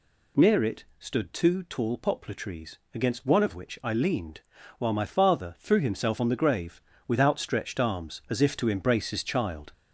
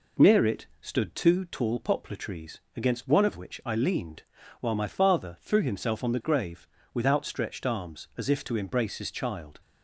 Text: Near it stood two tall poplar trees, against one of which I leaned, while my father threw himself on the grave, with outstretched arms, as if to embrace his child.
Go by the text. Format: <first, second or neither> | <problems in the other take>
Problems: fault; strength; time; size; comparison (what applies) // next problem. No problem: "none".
second | gets louder; noticeable; throughout; 4.5 dB // pauses between "it" and "stood"; slight; at 0.8 s; 0.16 s long; slight in the second